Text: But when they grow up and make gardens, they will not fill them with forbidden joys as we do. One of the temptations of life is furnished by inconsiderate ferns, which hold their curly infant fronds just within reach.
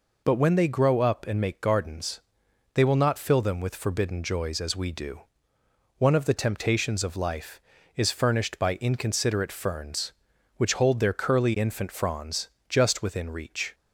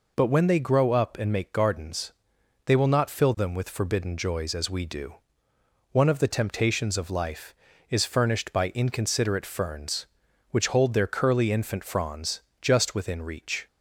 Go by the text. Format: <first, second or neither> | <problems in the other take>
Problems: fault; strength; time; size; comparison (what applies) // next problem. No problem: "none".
neither | pauses between "fronds" and "just"; slight; the same in both